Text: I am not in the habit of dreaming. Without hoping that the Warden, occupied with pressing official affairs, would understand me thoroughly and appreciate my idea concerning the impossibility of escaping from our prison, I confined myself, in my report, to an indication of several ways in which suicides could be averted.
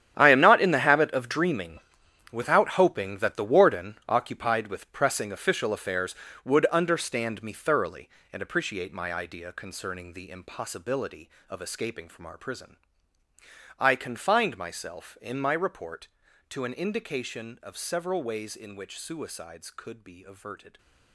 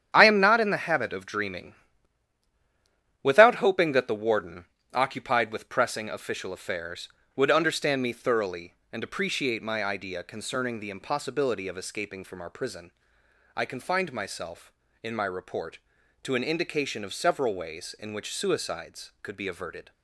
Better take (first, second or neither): second